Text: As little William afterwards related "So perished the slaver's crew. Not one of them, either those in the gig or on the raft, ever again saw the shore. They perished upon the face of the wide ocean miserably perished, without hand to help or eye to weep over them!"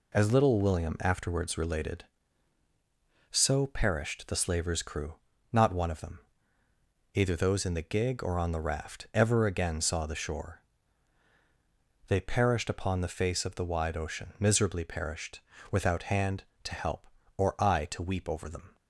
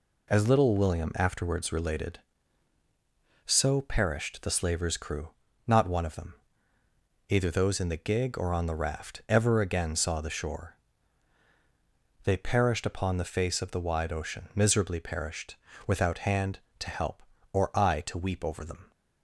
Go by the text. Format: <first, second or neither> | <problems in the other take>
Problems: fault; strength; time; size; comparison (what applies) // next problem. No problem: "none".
neither | none